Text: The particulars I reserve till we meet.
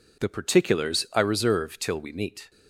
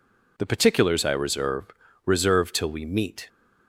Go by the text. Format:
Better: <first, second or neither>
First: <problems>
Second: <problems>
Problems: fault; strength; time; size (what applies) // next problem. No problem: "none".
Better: first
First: none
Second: says "reserve" twice; at 2.0 s